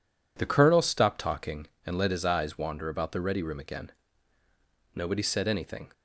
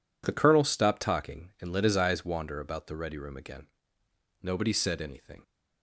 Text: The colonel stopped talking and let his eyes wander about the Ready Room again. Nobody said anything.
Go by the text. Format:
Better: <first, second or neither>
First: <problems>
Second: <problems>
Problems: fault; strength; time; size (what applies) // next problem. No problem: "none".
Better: neither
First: none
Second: none